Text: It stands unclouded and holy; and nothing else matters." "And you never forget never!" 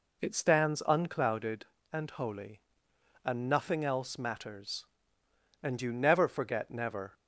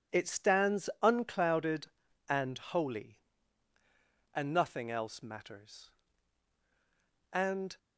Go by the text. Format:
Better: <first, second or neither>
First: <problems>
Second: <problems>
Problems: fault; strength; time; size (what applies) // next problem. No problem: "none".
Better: first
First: none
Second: stops before "you never forget never"; at 7.7 s